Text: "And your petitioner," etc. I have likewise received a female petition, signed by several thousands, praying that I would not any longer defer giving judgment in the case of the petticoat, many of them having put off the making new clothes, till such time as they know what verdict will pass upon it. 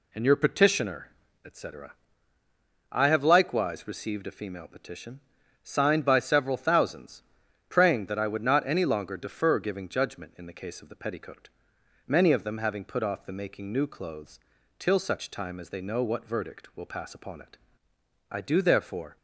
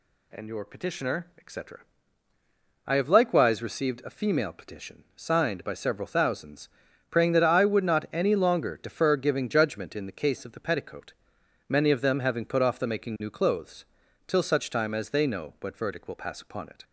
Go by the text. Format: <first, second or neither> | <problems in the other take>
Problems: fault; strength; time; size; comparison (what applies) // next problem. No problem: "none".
second | goes on to say "I do therefore"; noticeable; from 18.3 s on; 0.86 s long